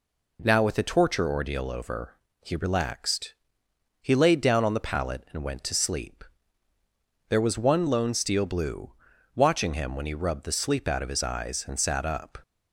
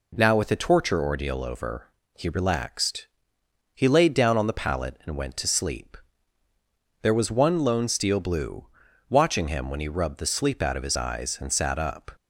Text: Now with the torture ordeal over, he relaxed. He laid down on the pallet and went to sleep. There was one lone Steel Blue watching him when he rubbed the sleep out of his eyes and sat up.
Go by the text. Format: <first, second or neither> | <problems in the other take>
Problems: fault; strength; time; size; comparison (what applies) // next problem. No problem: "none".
neither | pauses between "Blue" and "watching"; the same in both